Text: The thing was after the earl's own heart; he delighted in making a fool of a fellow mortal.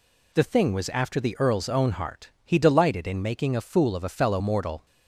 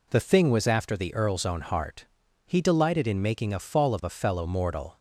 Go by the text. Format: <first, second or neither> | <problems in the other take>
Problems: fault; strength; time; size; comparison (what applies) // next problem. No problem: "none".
first | says "fall" for "fool"; at 3.5 s